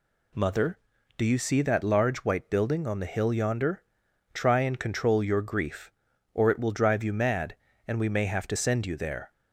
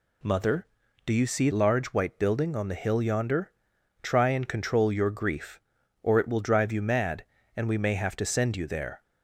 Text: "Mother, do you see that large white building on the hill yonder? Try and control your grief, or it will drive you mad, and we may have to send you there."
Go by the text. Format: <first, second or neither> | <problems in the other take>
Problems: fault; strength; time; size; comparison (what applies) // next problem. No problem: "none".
first | skips "that"; at 1.5 s